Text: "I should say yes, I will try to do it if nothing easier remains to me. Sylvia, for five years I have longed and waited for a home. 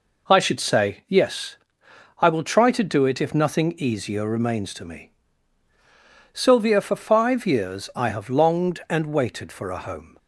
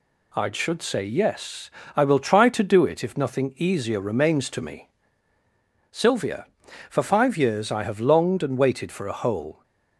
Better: first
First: none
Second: says "hole" for "home"; at 9.1 s

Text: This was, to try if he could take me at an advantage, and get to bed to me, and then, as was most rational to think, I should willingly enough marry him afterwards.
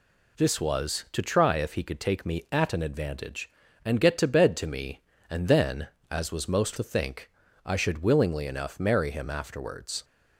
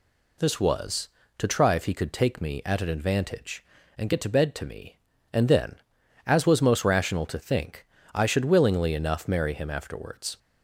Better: second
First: skips "rational"; at 6.7 s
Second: none

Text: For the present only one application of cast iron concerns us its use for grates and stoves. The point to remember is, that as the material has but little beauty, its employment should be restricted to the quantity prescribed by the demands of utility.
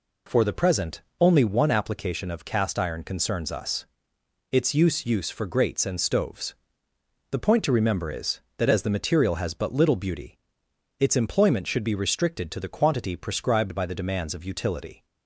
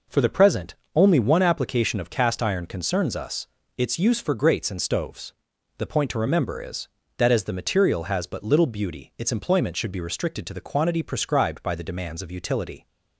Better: second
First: pauses between "present" and "only"; slight; at 1.0 s; 0.18 s long // pauses between "us" and "its"; noticeable; at 3.8 s; 0.66 s long // says "use" twice; at 5.0 s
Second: pauses between "present" and "only"; slight; at 0.7 s; 0.22 s long // pauses between "us" and "its"; slight; at 3.4 s; 0.30 s long

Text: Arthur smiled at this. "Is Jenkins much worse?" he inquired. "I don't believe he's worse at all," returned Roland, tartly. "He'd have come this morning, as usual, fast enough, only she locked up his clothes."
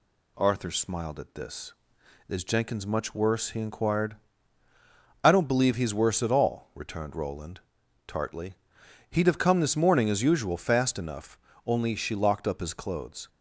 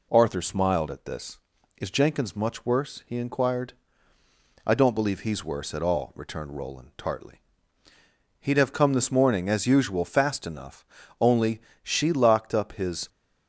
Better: first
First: none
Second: pauses between "only" and "she"; slight; at 11.6 s; 0.26 s long // stops before "clothes"; at 13.0 s

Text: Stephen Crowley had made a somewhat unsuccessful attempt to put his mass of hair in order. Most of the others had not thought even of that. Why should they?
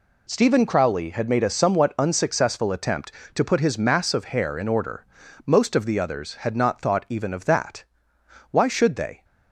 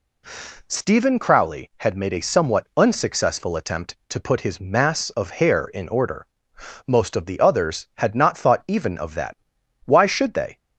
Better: neither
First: none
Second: none

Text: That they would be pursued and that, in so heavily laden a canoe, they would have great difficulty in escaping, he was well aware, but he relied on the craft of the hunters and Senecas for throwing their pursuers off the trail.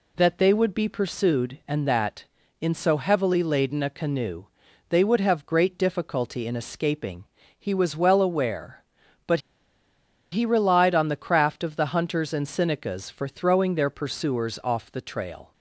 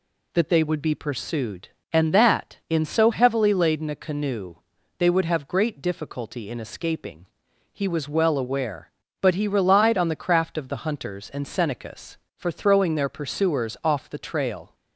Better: second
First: pauses between "but" and "he"; noticeable; at 9.3 s; 0.92 s long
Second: none

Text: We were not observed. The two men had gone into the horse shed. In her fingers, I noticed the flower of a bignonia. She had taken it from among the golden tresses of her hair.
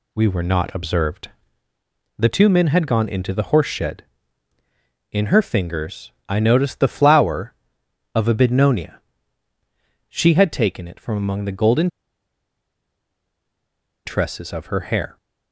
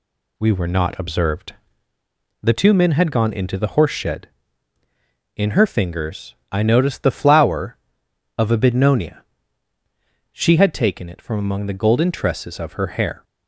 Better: second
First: pauses between "golden" and "tresses"; strong; at 11.8 s; 2.1 s long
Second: none

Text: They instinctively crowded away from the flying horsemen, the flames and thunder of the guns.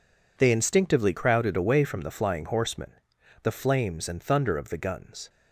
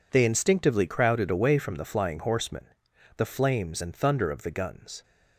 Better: neither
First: none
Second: none

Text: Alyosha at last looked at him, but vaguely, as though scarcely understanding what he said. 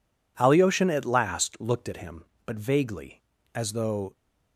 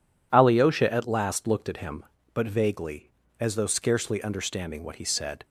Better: second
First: stops before "scarcely understanding what he said"; at 4.1 s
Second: none

